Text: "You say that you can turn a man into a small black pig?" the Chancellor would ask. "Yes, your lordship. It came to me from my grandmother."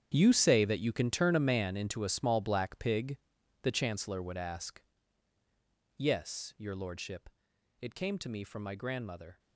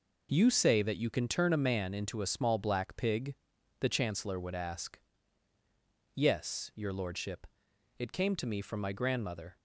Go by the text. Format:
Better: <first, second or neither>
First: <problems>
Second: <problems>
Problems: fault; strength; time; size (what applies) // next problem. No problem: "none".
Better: second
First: gets quieter; strong; throughout; 14.5 dB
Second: none